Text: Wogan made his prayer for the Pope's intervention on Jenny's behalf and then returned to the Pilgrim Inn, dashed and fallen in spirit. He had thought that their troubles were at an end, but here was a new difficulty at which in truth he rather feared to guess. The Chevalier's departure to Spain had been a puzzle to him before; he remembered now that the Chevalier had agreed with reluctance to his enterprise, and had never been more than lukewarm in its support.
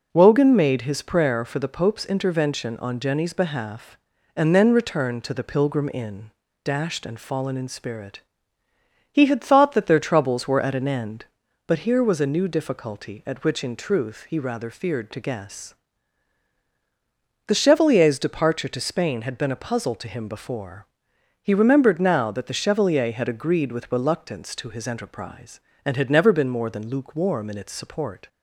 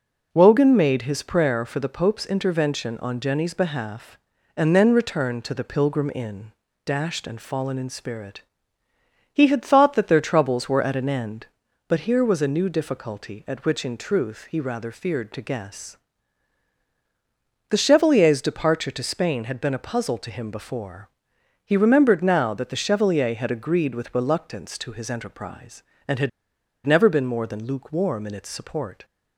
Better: first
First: none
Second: pauses between "had" and "never"; noticeable; at 26.2 s; 0.54 s long

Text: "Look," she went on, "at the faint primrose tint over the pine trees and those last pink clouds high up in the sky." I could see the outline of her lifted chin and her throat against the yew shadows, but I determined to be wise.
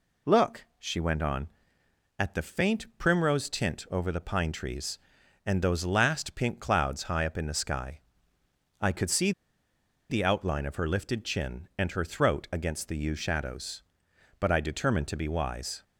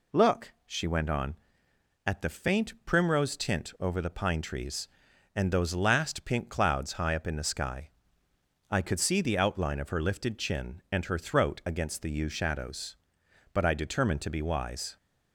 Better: second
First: pauses between "see" and "the"; noticeable; at 9.3 s; 0.78 s long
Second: none

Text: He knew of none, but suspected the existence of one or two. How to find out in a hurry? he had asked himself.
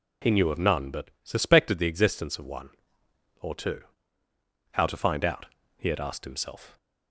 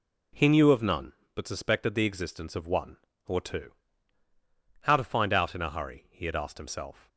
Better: second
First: skips "in a hurry"; at 5.6 s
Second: none

